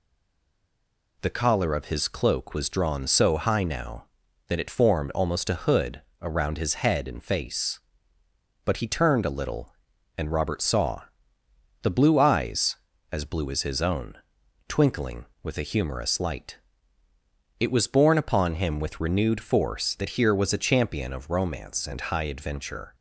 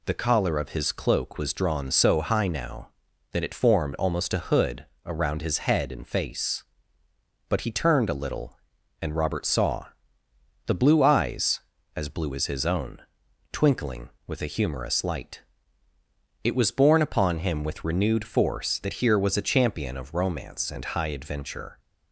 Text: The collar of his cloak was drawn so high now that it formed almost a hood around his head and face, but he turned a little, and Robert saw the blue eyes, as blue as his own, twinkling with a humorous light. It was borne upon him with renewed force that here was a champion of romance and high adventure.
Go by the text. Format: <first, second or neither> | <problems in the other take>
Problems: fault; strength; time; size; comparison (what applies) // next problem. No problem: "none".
second | stays silent before the first word; noticeable; until 1.1 s; 1.1 s long // pauses between "hood" and "around"; slight; at 6.0 s; 0.18 s long; slight in the second // pauses between "saw" and "the"; noticeable; at 11.0 s; 0.78 s long; noticeable in the second